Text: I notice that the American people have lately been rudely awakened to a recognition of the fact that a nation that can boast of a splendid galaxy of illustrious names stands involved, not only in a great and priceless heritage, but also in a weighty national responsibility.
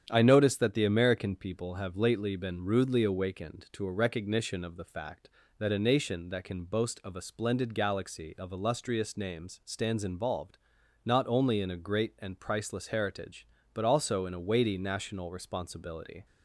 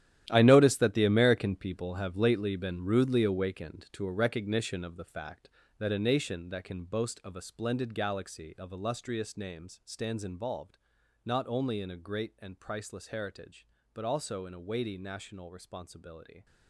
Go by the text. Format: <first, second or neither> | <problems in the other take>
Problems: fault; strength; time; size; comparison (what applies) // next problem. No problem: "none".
first | gets quieter; strong; throughout; 13.5 dB // starts louder than the rest; strong; until 1.3 s; 12 dB; strong in the first